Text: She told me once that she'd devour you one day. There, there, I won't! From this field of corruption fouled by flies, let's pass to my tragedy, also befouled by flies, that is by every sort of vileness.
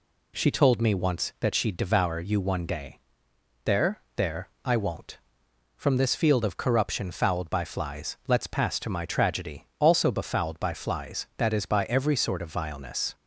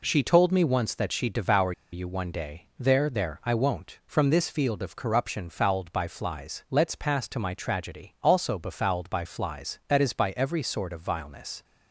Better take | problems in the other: first | pauses between "devour" and "you"; slight; at 1.7 s; 0.21 s long

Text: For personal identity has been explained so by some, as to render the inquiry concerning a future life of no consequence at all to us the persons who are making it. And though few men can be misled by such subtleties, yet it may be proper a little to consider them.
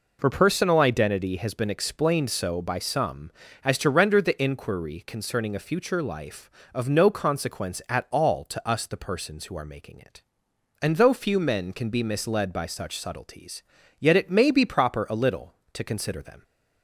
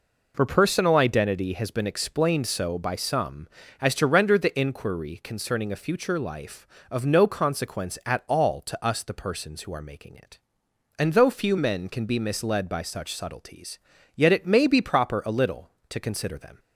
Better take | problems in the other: neither | none

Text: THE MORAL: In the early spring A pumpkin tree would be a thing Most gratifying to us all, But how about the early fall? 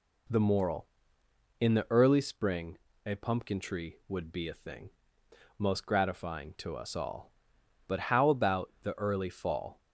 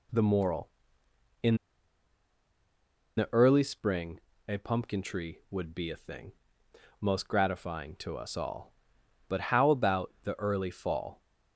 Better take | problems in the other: first | pauses between "In" and "the"; strong; at 1.5 s; 1.6 s long // pauses between "spring" and "A"; slight; at 4.1 s; 0.30 s long; slight in the first // pauses between "thing" and "Most"; noticeable; at 6.3 s; 0.68 s long; noticeable in the first

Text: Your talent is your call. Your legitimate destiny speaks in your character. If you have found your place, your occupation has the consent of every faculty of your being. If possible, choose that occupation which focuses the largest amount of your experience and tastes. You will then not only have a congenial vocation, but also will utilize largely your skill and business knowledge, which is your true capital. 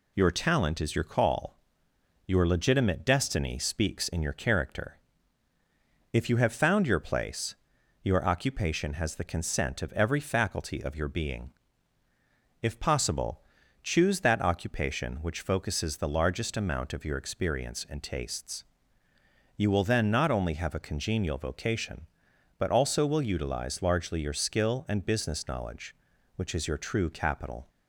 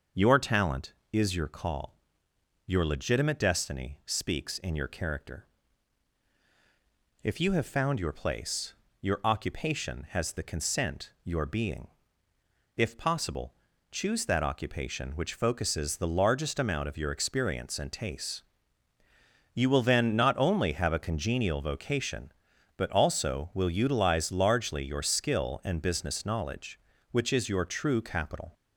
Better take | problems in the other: first | starts louder than the rest; until 1.3 s; 6 dB // skips "of every faculty of"; at 11.1 s

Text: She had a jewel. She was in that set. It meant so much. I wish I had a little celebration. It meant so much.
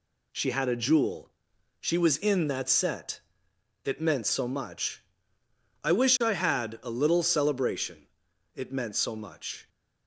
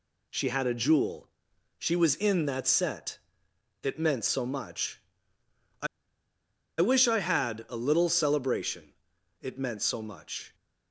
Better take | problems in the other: first | pauses between "I" and "wish"; noticeable; at 5.8 s; 0.93 s long

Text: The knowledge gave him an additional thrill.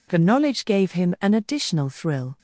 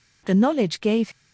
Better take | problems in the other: first | stops before "him an additional thrill"; at 1.1 s

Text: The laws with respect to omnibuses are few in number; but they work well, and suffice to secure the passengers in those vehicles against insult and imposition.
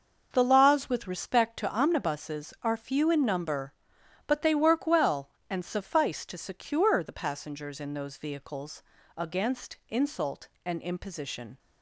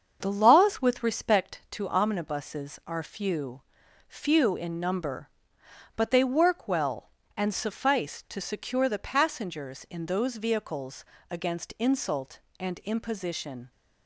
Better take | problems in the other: first | starts louder than the rest; until 1.2 s; 7 dB // says "few" twice; at 4.0 s // pauses between "vehicles" and "against"; slight; at 11.0 s; 0.26 s long; slight in the first

